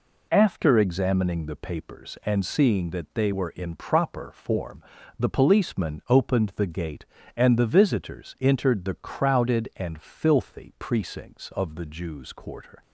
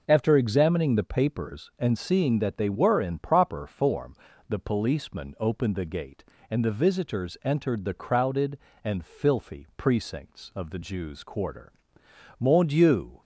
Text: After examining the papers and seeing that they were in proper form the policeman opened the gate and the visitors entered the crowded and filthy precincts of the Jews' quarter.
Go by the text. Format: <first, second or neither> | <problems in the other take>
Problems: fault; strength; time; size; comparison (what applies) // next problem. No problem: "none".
first | pauses between "form" and "the"; slight; at 4.1 s; 0.34 s long; slight in the first // goes on to say "Mon Dieu"; noticeable; from 12.3 s on; 0.82 s long